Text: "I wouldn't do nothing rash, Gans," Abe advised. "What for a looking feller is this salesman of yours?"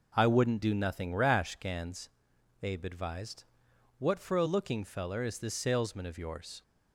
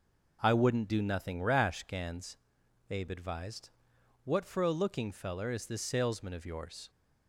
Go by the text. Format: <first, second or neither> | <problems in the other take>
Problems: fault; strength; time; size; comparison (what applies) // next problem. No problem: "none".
neither | none